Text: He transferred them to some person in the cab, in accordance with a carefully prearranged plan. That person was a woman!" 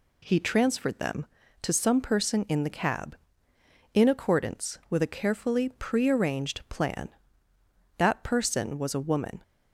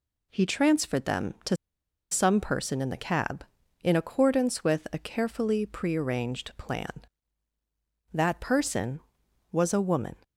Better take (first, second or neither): first